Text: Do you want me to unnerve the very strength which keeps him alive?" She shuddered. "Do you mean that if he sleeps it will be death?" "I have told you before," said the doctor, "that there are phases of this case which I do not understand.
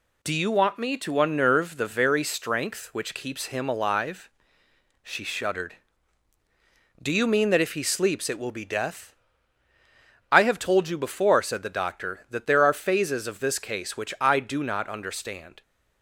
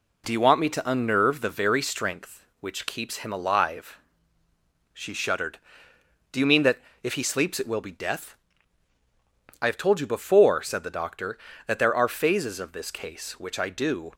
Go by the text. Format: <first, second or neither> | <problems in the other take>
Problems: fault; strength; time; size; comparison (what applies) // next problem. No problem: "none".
first | pauses between "that" and "if"; slight; at 6.8 s; 0.22 s long // stops before "not understand"; at 14.1 s